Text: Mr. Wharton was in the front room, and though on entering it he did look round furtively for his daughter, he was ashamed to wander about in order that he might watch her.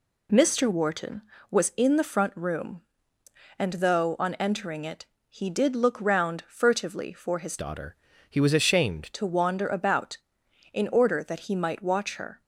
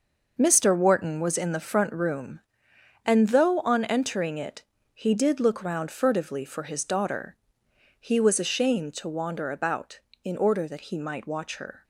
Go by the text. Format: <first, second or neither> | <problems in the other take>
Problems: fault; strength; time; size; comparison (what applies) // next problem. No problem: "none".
second | pauses between "it" and "he"; slight; at 5.0 s; 0.24 s long; slight in the second // changes voice from "daughter" to "ashamed"; from 7.5 to 9.0 s; 1.5 s long